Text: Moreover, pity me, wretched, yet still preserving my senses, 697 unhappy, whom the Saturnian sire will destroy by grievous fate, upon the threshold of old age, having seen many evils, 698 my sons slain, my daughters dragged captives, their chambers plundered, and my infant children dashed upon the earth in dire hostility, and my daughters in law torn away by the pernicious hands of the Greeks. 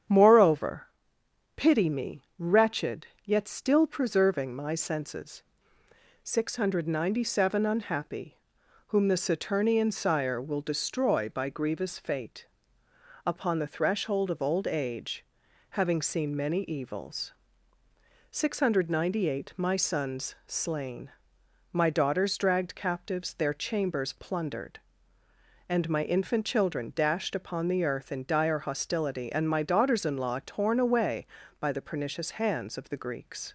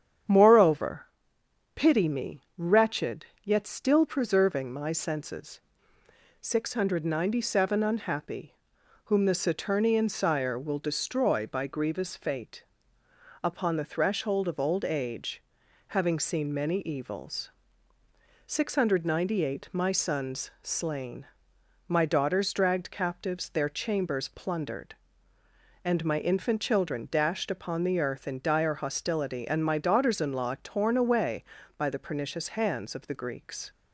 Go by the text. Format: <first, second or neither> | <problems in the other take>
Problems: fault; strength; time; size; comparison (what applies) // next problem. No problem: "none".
neither | starts louder than the rest; strong; the same in both